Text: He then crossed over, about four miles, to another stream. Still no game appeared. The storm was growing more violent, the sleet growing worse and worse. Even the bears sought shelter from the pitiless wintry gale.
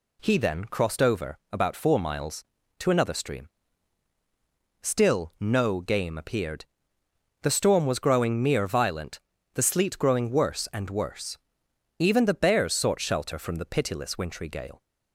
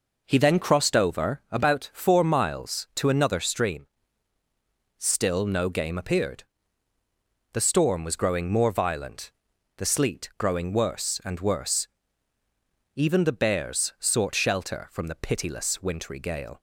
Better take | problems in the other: second | says "mere" for "more"; at 8.4 s

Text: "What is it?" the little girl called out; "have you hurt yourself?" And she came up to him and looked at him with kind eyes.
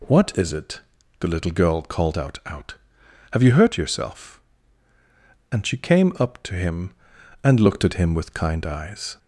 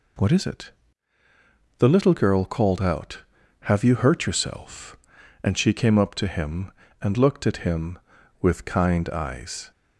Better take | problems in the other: second | says "out" twice; at 2.4 s

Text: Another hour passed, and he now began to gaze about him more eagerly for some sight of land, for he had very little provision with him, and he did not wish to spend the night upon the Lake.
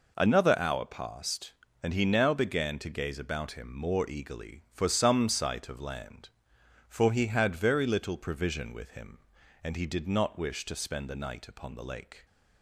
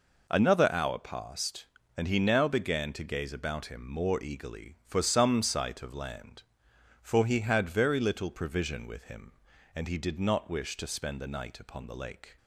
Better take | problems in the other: neither | none

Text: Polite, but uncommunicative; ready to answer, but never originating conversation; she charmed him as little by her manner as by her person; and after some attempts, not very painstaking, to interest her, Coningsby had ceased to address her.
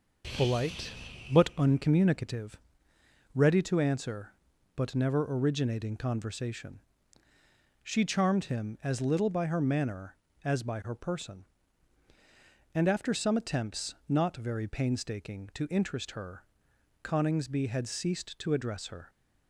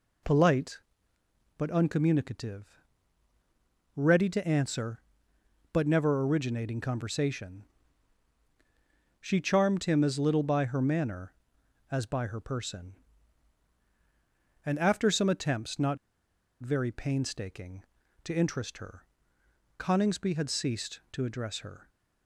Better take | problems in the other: first | pauses between "not" and "very"; noticeable; at 15.9 s; 0.62 s long

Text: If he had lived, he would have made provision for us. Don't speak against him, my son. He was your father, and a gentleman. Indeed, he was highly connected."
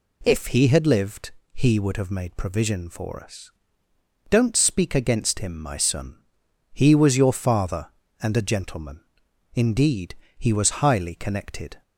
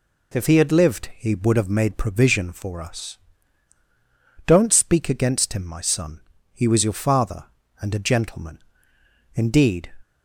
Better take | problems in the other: first | stops before "he was highly connected"; at 10.0 s

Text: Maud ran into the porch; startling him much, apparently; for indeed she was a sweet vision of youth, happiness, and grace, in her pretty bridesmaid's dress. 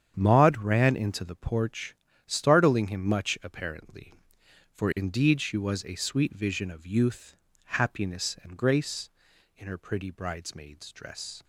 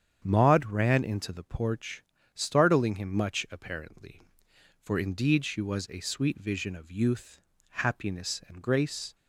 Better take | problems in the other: first | starts louder than the rest; strong; until 1.2 s; 8 dB; strong in the first // stops before "in her pretty bridesmaid's dress"; at 9.1 s

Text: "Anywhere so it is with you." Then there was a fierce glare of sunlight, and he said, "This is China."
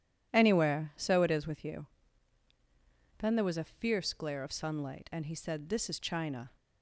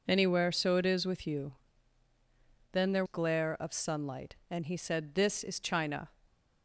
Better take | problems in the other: first | skips "was a fierce"; at 3.0 s

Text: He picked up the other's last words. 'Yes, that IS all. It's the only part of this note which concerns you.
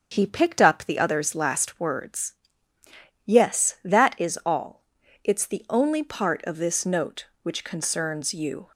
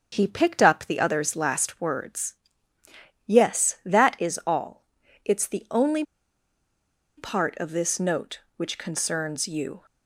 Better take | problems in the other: first | starts louder than the rest; until 1.1 s; 7 dB; also in the first // pauses between "only" and "part"; at 6.0 s; 1.1 s long

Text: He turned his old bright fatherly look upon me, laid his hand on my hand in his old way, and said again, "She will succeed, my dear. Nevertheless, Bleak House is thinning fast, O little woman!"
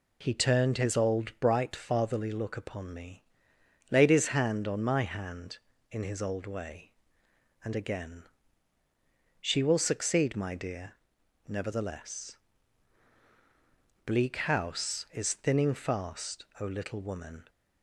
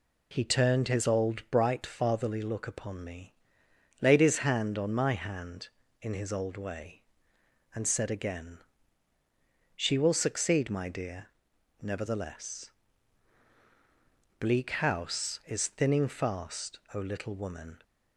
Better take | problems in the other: second | skips "said"; at 7.7 s

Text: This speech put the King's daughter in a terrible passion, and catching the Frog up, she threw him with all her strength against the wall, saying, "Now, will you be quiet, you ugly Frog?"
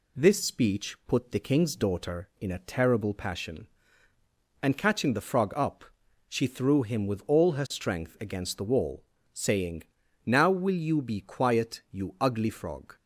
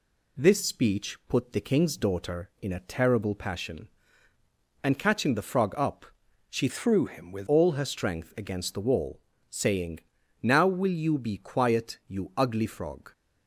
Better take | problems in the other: first | changes voice from "threw" to "with"; from 6.6 to 7.4 s; 0.8 s long

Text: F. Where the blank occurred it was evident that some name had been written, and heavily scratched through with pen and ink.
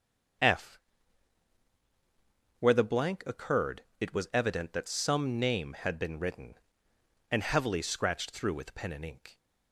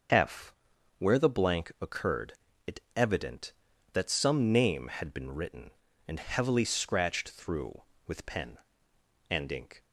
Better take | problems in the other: first | starts louder than the rest; until 1.5 s; 6.5 dB; also in the first // pauses between "occurred" and "it"; slight; at 2.3 s; 0.34 s long; slight in the first // skips "was"; at 2.8 s

